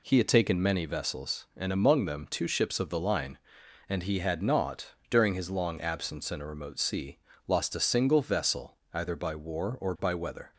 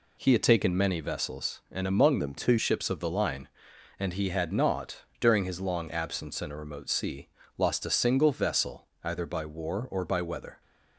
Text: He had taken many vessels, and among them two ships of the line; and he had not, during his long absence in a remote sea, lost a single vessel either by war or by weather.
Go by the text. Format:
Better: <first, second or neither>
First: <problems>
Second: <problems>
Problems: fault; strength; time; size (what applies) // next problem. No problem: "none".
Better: first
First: pauses between "vessel" and "either"; slight; at 8.7 s; 0.16 s long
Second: changes voice from "them" to "two"; from 2.1 to 2.5 s; 0.4 s long // pauses between "vessel" and "either"; slight; at 8.8 s; 0.16 s long